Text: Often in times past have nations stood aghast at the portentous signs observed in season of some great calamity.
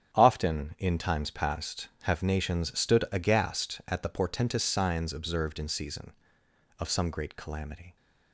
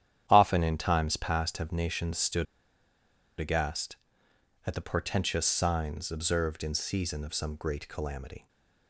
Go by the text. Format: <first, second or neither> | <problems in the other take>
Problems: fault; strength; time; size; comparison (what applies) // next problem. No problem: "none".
first | starts louder than the rest; strong; until 1.2 s; 10 dB; strong in the first // pauses between "stood" and "aghast"; noticeable; at 2.4 s; 0.94 s long // stays silent after the last word; slight; from 8.3 s on; 0.5 s long